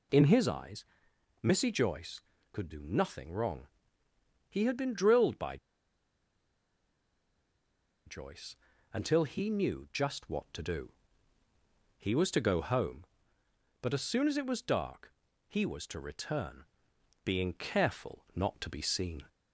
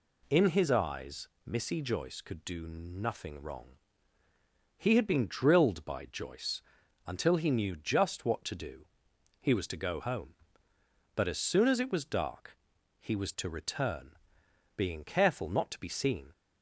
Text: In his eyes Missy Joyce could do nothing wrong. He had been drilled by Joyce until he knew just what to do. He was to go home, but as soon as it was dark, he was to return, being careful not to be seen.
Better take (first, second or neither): second